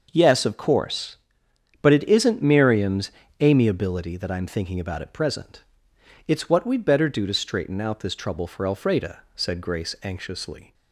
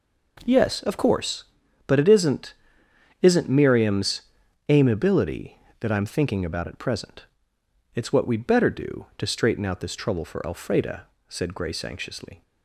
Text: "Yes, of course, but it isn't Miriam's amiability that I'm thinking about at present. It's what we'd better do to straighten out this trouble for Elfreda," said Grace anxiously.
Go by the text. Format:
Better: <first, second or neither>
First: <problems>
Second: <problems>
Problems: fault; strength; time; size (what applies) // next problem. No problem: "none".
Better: first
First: pauses between "Miriam's" and "amiability"; slight; at 3.1 s; 0.30 s long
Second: says "isn't" twice; at 3.2 s // pauses between "Miriam's" and "amiability"; noticeable; at 4.2 s; 0.48 s long